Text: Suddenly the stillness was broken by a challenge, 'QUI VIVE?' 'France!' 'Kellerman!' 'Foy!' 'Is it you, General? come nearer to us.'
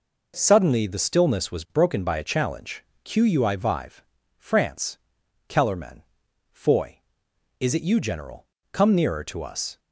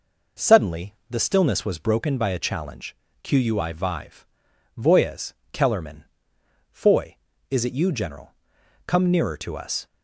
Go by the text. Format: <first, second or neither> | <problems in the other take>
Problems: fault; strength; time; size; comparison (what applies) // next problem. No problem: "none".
first | pauses between "Suddenly" and "the"; slight; at 0.9 s; 0.16 s long // says "Voyez" for "France"; at 4.7 s